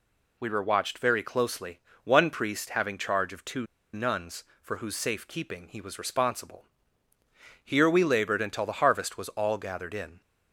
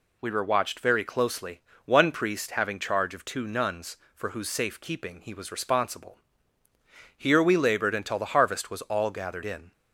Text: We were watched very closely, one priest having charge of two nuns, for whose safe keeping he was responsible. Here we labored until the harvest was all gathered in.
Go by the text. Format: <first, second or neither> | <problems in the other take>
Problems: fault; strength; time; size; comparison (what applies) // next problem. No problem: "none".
second | pauses between "two" and "nuns"; slight; at 3.6 s; 0.28 s long